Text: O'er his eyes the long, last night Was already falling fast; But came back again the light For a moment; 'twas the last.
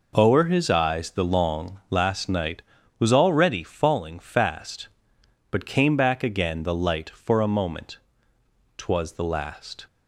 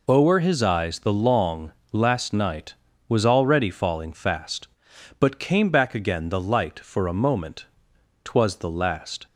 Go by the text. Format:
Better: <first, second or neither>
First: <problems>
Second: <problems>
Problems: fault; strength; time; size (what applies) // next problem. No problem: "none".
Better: neither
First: none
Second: none